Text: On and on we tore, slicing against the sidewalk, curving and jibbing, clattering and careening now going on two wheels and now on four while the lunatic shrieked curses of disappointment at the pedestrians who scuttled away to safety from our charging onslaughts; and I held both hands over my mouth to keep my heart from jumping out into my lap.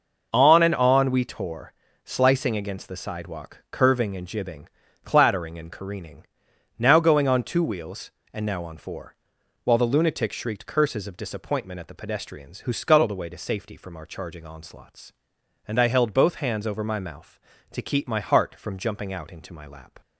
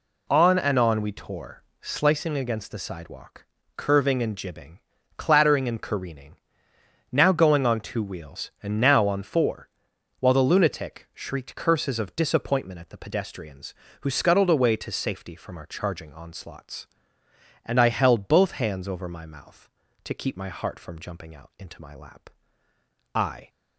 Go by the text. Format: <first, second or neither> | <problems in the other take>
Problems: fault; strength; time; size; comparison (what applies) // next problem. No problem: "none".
first | pauses between "careening" and "now"; noticeable; at 6.3 s; 0.74 s long; noticeable in the first // pauses between "four" and "while"; noticeable; at 9.6 s; 0.52 s long; noticeable in the first // goes on to say "I"; slight; from 23.1 s on; 0.34 s long